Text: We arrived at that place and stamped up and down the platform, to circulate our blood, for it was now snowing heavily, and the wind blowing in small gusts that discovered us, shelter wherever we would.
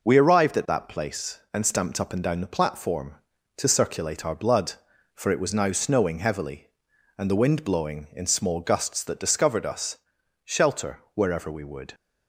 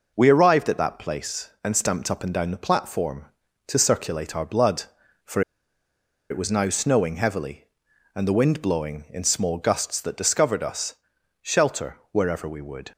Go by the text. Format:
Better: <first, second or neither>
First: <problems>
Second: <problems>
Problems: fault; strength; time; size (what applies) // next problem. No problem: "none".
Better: first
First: pauses between "shelter" and "wherever"; slight; at 10.9 s; 0.16 s long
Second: pauses between "for" and "it"; noticeable; at 5.4 s; 0.89 s long // pauses between "shelter" and "wherever"; slight; at 11.9 s; 0.16 s long